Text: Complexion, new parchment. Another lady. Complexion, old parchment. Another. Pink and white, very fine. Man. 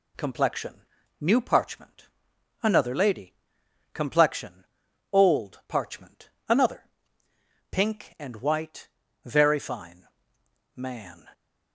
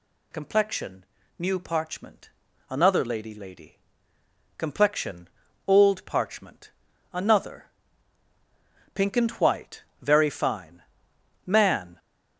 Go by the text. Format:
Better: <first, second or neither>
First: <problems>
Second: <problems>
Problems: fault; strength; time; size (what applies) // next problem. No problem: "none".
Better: first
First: none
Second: says "lady" twice; at 3.3 s